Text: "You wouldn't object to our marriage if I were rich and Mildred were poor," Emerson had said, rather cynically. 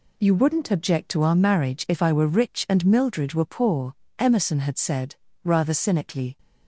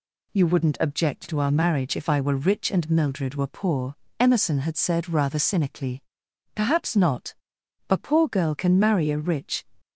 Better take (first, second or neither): first